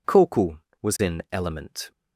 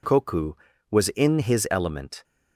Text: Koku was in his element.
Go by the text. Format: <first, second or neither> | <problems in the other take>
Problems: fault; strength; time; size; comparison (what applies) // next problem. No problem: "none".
second | skips "his"; at 1.2 s